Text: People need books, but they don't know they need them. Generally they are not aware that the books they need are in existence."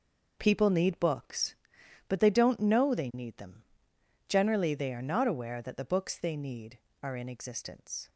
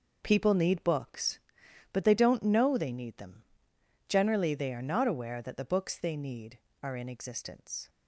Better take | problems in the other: neither | none

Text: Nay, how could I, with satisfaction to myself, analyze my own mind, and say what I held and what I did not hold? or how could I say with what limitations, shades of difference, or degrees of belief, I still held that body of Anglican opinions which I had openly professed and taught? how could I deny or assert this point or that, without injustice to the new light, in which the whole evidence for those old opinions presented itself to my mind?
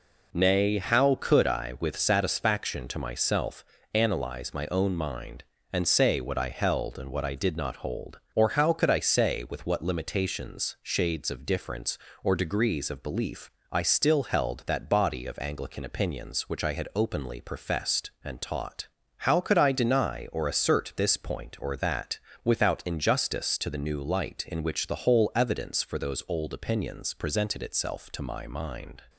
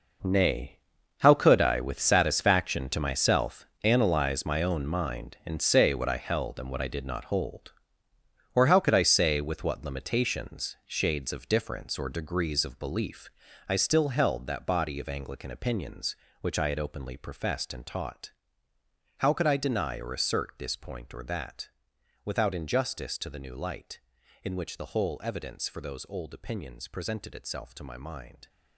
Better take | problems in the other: first | gets quieter; strong; throughout; 13 dB

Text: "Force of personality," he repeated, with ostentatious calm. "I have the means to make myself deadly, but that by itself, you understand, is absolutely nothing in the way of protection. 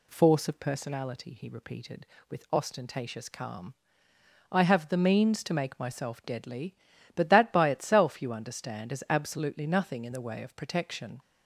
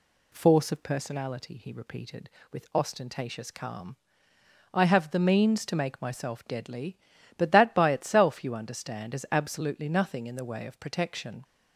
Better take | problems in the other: neither | none

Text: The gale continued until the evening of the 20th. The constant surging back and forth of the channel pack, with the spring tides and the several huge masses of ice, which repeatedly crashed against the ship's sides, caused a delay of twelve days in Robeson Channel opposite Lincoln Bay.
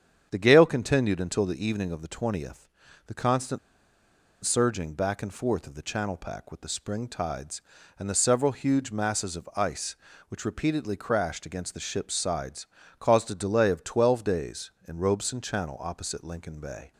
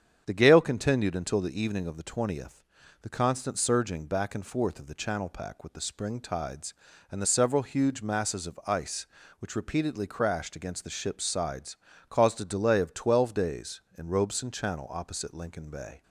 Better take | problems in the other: second | starts louder than the rest; strong; until 1.3 s; 8 dB; strong in the second // pauses between "constant" and "surging"; noticeable; at 3.5 s; 0.85 s long

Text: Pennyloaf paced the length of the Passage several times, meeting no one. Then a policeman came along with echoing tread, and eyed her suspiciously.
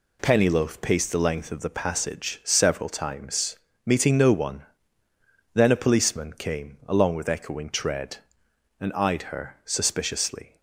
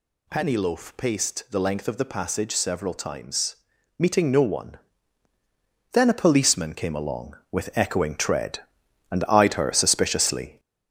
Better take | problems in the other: first | gets louder; noticeable; throughout; 4.5 dB

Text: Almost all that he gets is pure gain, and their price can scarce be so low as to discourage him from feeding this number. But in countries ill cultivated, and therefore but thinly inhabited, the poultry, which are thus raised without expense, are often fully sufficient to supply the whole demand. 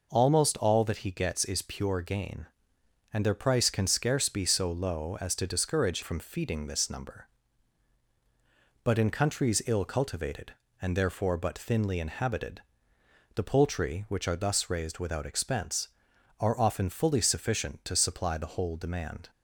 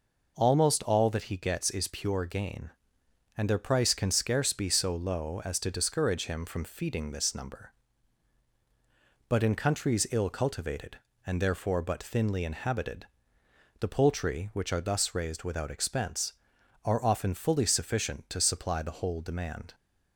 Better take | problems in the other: second | skips "him"; at 6.0 s

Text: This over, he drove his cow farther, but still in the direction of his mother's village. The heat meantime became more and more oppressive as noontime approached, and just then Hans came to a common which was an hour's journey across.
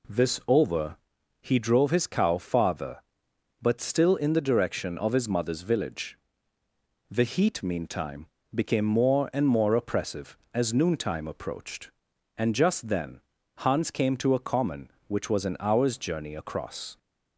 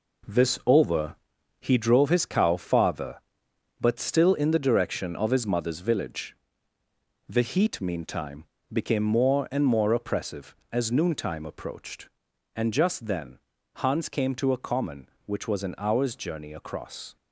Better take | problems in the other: first | gets quieter; throughout; 7 dB // pauses between "meantime" and "became"; slight; at 8.4 s; 0.28 s long; slight in the first // pauses between "then" and "Hans"; at 13.3 s; 0.38 s long; also in the first

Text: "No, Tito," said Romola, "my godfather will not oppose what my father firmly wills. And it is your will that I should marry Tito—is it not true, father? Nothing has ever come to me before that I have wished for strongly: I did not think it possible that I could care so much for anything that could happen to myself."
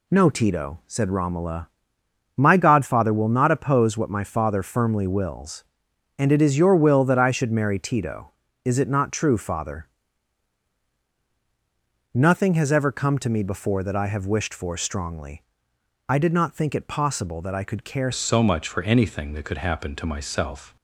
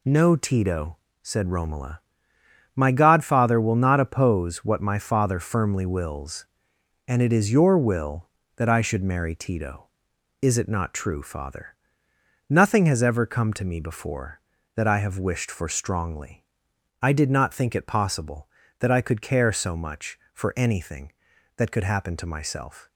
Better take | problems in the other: second | changes voice at "so"; from 18.1 s on; 2.6 s long

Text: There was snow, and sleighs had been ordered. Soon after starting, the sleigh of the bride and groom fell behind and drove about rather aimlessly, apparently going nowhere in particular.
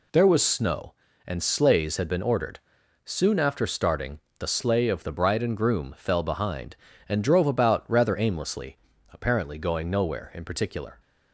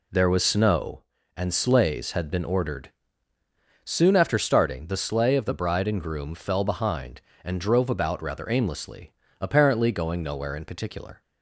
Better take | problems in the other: neither | none

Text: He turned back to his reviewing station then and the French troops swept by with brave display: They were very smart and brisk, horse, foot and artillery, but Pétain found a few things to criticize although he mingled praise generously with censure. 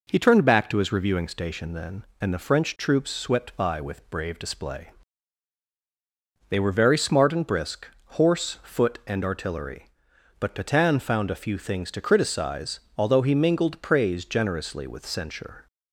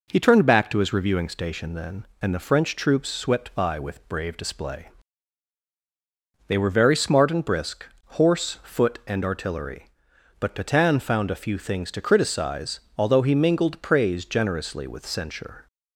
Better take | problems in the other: neither | pauses between "criticize" and "although"; slight; the same in both

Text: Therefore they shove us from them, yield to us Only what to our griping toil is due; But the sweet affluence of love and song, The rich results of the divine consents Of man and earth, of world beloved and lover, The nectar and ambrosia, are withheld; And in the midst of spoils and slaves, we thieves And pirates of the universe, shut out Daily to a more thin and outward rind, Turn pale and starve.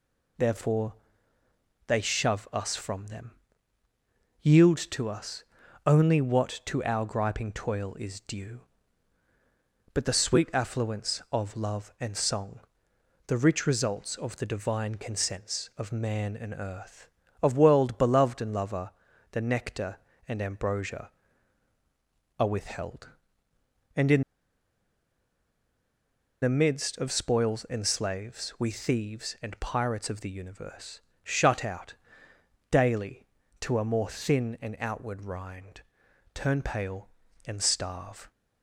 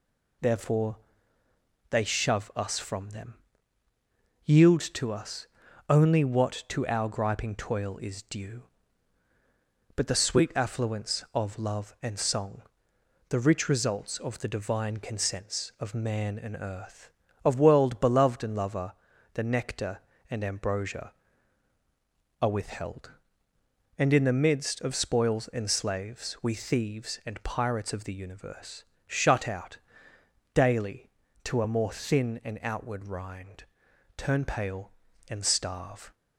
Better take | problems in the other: second | pauses between "Therefore" and "they"; noticeable; at 0.9 s; 0.92 s long; noticeable in the second // pauses between "us" and "Only"; at 5.4 s; 0.42 s long; also in the second // pauses between "in" and "the"; strong; at 24.2 s; 2.2 s long // pauses between "out" and "Daily"; noticeable; at 31.9 s; 0.76 s long; noticeable in the second

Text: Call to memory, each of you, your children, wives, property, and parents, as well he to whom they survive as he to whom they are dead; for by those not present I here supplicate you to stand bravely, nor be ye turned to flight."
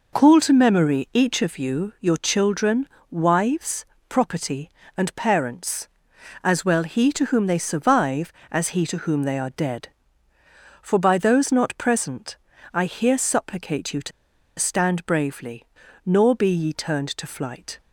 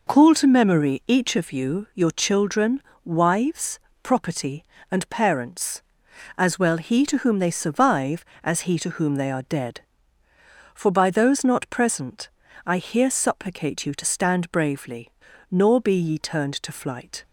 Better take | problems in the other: second | pauses between "present" and "I"; slight; at 12.3 s; 0.36 s long; slight in the second // pauses between "to" and "stand"; noticeable; at 14.1 s; 0.48 s long

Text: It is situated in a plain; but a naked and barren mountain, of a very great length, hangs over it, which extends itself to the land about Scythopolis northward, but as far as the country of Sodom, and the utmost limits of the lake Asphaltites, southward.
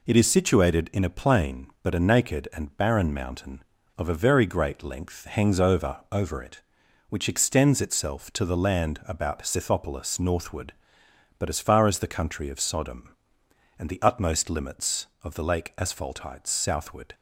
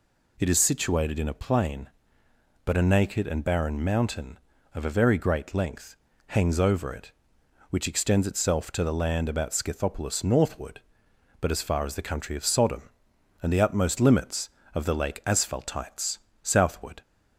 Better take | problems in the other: second | says "over" twice; at 6.1 s

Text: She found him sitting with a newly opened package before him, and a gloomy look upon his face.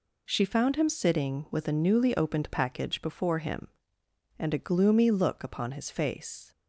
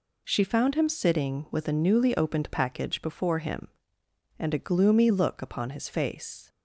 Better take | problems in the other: neither | none

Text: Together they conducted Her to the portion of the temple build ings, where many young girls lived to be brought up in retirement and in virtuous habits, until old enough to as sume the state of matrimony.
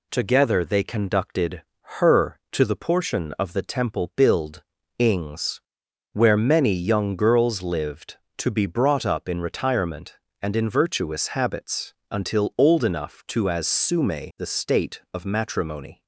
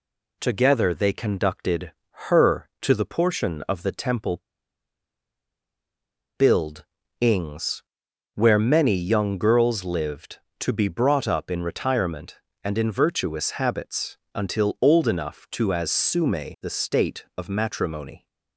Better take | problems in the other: first | pauses between "conducted" and "Her"; slight; at 1.9 s; 0.36 s long; slight in the first // pauses between "temple" and "build"; strong; at 4.3 s; 1.9 s long // pauses between "build" and "ings"; slight; at 6.8 s; 0.34 s long; slight in the first

